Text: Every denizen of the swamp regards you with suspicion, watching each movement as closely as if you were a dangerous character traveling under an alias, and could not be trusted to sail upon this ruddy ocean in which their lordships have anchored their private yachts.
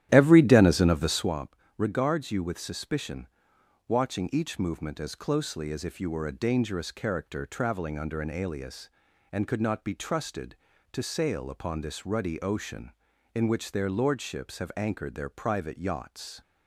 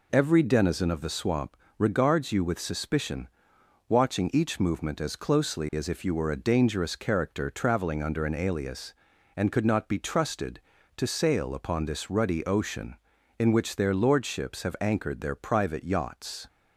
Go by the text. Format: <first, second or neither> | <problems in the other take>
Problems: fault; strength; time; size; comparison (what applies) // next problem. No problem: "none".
second | starts louder than the rest; strong; until 1.3 s; 12 dB // pauses between "swamp" and "regards"; slight; at 1.5 s; 0.22 s long; slight in the second